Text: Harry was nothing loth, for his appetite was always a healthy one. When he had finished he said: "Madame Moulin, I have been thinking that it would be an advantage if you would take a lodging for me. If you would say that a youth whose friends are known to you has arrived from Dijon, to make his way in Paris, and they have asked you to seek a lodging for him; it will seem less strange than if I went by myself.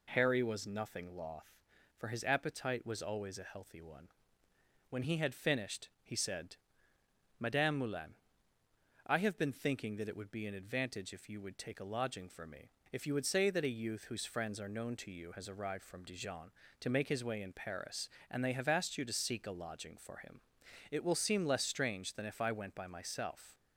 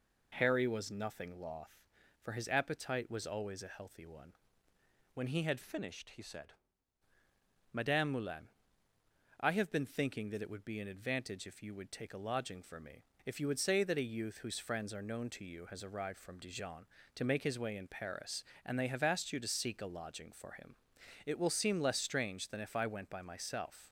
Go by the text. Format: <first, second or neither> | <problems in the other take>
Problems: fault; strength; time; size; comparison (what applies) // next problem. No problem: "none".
first | changes voice from "finished" to "said"; from 5.6 to 6.5 s; 0.9 s long